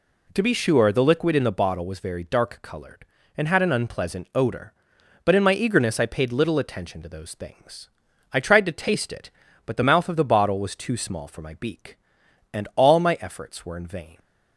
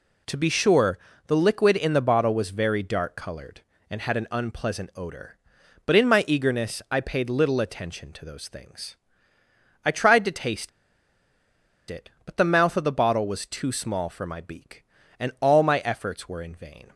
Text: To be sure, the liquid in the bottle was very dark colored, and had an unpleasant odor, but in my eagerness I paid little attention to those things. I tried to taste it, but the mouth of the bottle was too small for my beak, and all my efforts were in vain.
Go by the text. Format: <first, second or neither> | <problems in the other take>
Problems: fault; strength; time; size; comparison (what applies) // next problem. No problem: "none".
first | pauses between "taste" and "it"; at 10.6 s; 1.2 s long